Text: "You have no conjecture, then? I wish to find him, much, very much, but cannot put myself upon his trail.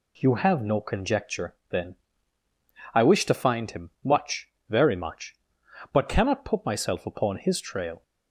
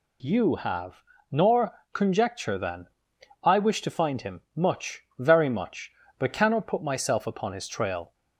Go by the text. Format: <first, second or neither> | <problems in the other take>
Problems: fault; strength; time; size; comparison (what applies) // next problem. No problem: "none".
first | says "nor" for "no"; at 1.3 s